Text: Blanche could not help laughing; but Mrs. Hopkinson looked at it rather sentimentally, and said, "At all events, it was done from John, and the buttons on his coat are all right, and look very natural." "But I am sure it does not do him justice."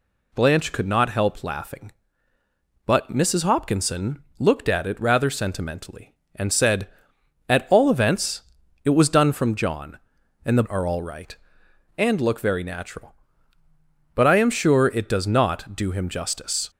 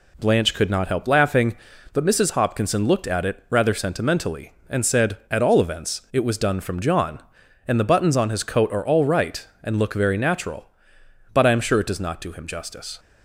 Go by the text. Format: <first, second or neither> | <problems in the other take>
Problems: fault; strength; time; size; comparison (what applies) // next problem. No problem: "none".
second | pauses between "Hopkinson" and "looked"; slight; at 4.2 s; 0.16 s long // skips "buttons on his coat"; at 10.6 s